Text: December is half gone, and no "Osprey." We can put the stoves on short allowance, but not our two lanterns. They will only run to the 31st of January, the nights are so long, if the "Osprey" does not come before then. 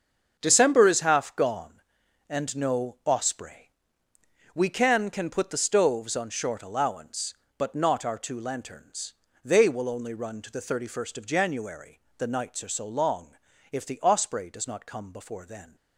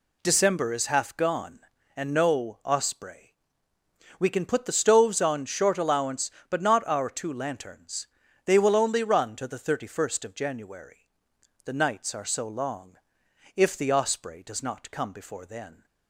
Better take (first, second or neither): second